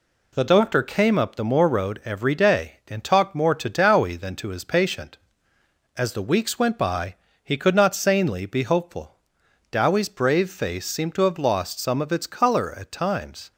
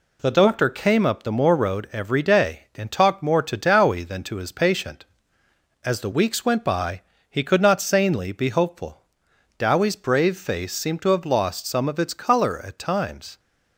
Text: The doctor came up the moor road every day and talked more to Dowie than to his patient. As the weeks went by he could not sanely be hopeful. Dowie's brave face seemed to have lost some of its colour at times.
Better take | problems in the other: neither | pauses between "by" and "he"; slight; the same in both

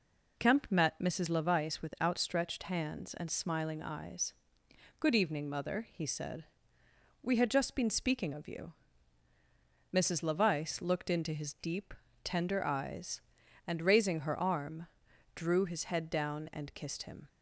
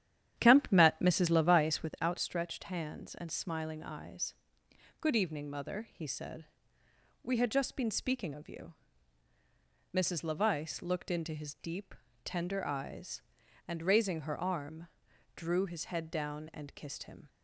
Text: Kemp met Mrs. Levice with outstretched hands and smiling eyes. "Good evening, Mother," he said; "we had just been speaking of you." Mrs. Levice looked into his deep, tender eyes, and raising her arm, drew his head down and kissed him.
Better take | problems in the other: first | starts louder than the rest; strong; until 2.1 s; 10 dB

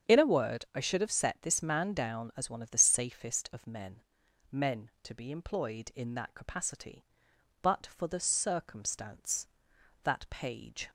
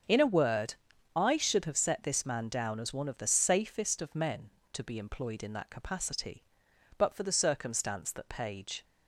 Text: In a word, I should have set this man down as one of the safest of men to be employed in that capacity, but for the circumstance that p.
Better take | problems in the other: second | starts louder than the rest; strong; until 1.1 s; 7.5 dB; also in the second // says "men" twice; at 4.5 s

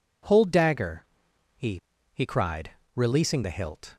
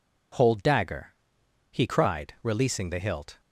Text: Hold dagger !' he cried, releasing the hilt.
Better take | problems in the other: second | says "he" twice; at 2.1 s

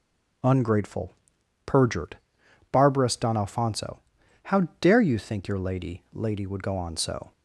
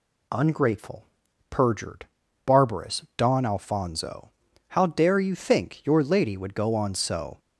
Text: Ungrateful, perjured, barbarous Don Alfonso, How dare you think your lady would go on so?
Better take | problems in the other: second | starts louder than the rest; strong; until 1.9 s; 7.5 dB // says "lady" twice; at 6.1 s

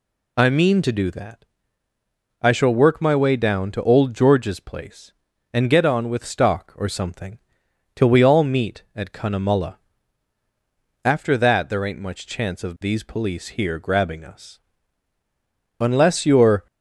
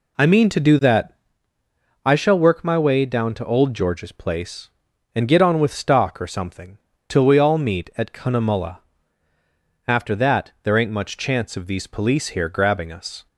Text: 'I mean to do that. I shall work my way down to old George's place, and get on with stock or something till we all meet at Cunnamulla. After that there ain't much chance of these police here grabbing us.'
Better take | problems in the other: second | pauses between "something" and "till"; noticeable; at 7.3 s; 0.56 s long; slight in the second // goes on to say "Unless you're"; noticeable; from 15.8 s on; 0.86 s long

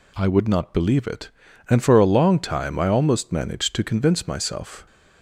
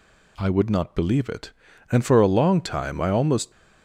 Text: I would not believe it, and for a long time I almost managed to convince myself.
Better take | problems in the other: first | stops before "managed to convince myself"; at 3.5 s

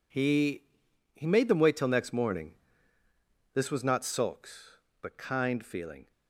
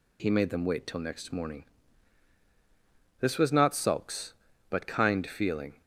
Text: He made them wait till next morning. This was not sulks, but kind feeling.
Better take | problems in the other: second | says "He" twice; at 1.1 s

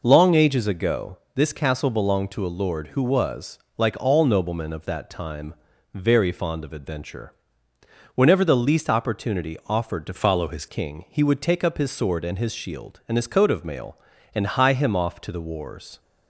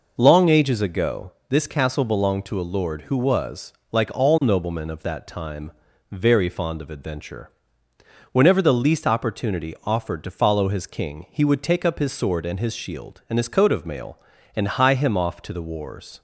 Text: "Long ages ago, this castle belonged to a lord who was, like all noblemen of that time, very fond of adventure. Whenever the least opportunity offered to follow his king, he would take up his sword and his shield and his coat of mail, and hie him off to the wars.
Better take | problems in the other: second | changes voice from "follow" to "his"; from 10.1 to 10.6 s; 0.5 s long

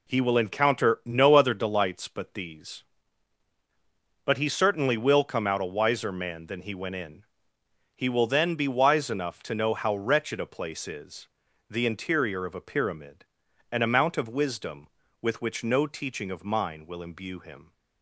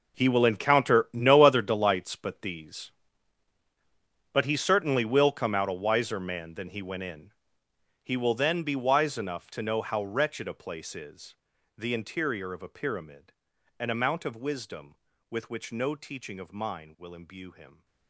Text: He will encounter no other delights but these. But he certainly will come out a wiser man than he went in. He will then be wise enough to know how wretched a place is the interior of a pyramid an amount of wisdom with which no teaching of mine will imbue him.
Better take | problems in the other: first | gets quieter; strong; throughout; 15 dB // pauses between "is" and "the"; at 11.3 s; 0.42 s long; also in the first // pauses between "pyramid" and "an"; at 13.3 s; 0.44 s long; also in the first

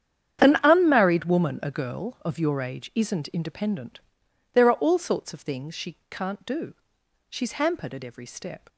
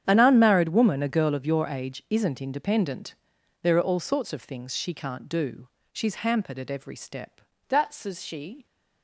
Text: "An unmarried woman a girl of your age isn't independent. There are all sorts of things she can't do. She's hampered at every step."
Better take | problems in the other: first | starts louder than the rest; strong; until 1.0 s; 9 dB; strong in the first // goes on to say "That's as she"; noticeable; from 7.6 s on; 0.98 s long

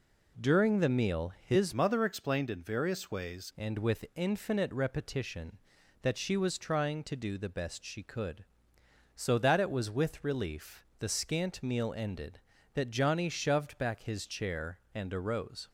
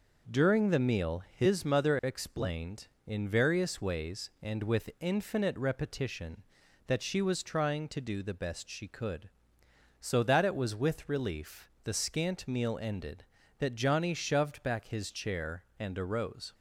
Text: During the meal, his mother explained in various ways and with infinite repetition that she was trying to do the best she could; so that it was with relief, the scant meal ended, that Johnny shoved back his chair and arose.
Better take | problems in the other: second | changes voice from "mother" to "ways"; from 1.7 to 3.5 s; 1.8 s long

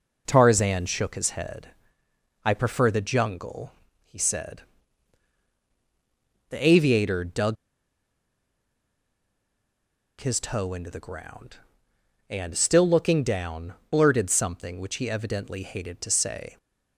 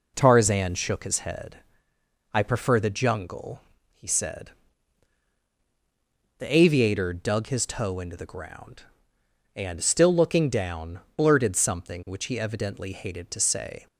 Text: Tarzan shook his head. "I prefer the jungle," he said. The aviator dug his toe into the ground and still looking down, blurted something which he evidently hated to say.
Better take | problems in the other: second | pauses between "dug" and "his"; strong; at 7.5 s; 2.6 s long

